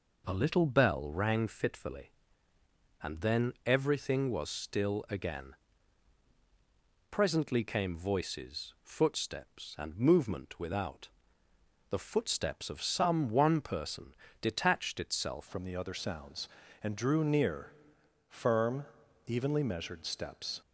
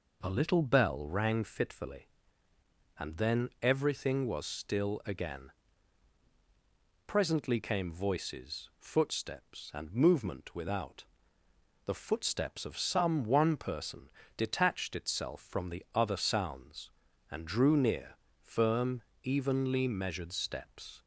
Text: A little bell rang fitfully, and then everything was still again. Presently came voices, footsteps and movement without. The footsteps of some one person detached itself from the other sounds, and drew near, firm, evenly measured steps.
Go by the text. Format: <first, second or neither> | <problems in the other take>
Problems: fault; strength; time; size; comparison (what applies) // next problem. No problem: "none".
second | pauses between "person" and "detached"; slight; at 14.1 s; 0.26 s long; slight in the second // changes voice at "from"; from 15.4 s on; 5.2 s long